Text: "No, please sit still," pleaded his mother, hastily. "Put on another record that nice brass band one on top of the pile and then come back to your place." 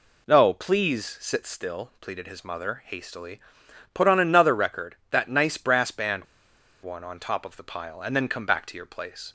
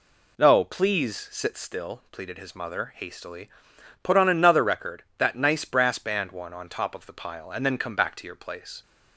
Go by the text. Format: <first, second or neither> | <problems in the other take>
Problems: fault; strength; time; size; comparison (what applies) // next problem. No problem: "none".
second | pauses between "band" and "one"; noticeable; at 6.2 s; 0.58 s long